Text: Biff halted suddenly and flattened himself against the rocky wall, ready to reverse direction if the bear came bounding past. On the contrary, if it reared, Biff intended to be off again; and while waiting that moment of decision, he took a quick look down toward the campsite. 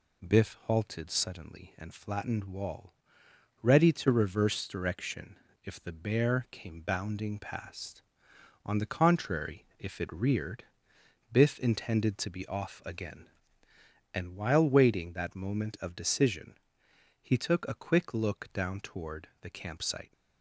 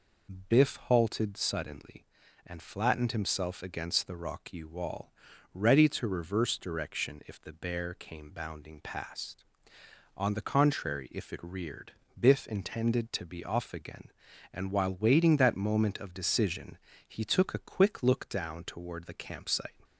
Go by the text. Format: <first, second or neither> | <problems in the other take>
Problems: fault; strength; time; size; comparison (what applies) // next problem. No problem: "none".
second | skips "himself against the rocky"; at 2.4 s // pauses between "direction" and "if"; slight; at 5.3 s; 0.30 s long